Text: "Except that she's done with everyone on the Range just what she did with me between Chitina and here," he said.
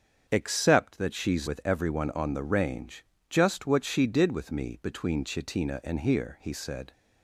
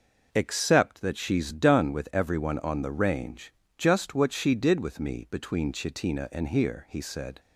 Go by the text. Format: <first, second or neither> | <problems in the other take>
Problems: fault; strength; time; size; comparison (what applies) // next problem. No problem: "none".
second | starts louder than the rest; until 1.2 s; 7 dB // skips "done"; at 1.4 s // pauses between "Range" and "just"; slight; at 3.0 s; 0.26 s long; slight in the second